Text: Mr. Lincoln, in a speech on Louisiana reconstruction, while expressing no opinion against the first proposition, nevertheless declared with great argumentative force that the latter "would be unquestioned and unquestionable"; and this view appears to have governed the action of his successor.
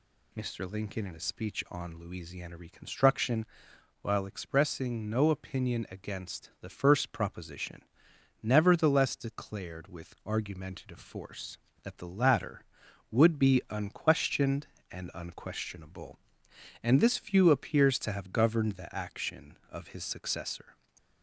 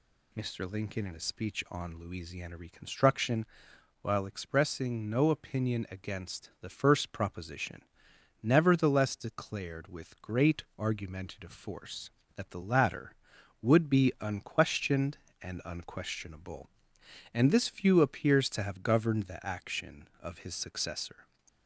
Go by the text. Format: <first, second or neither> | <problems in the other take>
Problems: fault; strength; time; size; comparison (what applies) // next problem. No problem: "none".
second | skips "great"; at 10.2 s // stays silent after the last word; slight; from 20.7 s on; 0.5 s long